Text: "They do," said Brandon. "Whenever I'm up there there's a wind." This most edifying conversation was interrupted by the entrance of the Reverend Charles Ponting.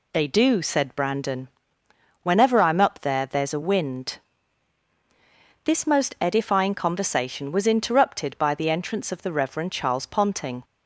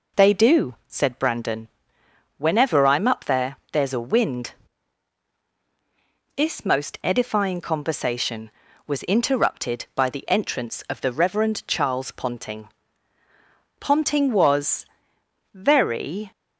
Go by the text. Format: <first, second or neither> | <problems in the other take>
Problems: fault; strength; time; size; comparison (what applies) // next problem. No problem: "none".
first | pauses between "there" and "there's"; slight; at 3.5 s; 0.16 s long // goes on to say "Ponting was very"; strong; from 13.7 s on; 2.5 s long